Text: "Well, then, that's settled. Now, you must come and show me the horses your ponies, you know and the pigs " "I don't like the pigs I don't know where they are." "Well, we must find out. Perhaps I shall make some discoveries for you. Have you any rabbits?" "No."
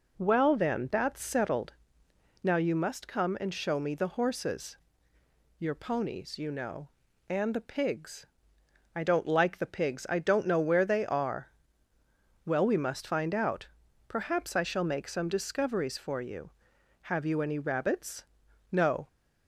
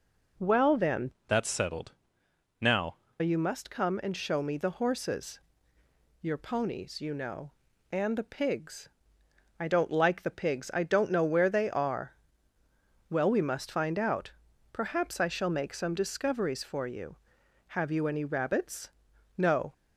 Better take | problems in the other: first | changes voice from "that's" to "Now"; from 1.2 to 2.9 s; 1.7 s long // pauses between "horses" and "your"; noticeable; at 5.4 s; 0.80 s long; noticeable in the first

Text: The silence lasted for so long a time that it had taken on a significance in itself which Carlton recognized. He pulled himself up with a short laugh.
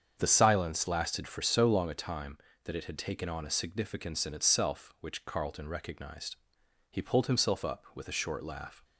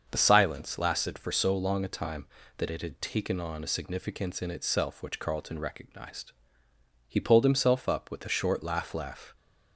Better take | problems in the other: first | starts louder than the rest; until 1.1 s; 6.5 dB; strong in the first // says "laugh" twice; at 8.9 s

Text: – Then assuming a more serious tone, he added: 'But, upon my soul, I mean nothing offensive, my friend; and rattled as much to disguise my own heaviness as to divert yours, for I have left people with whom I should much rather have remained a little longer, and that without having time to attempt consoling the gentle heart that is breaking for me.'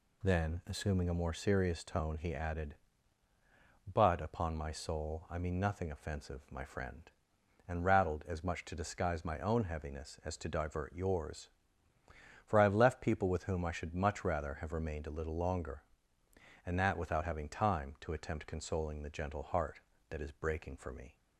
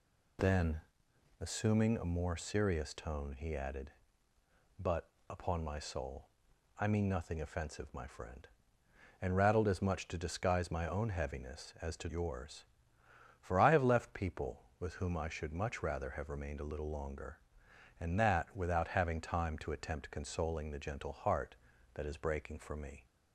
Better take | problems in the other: first | pauses between "Then" and "assuming"; noticeable; at 0.7 s; 0.58 s long // skips "divert"; at 12.0 s

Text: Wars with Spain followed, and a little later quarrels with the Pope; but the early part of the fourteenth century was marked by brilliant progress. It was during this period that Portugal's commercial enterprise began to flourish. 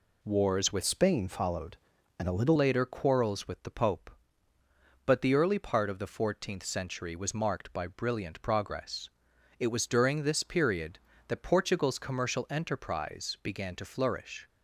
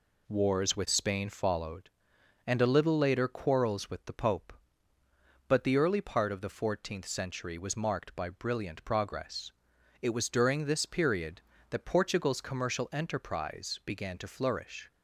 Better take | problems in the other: second | changes voice from "Spain" to "little"; from 0.8 to 2.5 s; 1.7 s long

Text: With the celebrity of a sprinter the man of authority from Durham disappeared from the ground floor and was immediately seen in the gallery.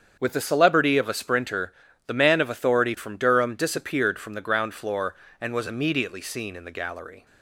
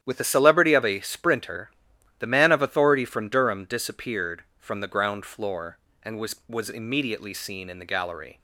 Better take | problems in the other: first | starts louder than the rest; strong; until 1.0 s; 10.5 dB; strong in the first // pauses between "sprinter" and "the"; noticeable; at 1.7 s; 0.50 s long; slight in the first // says "was" twice; at 6.4 s

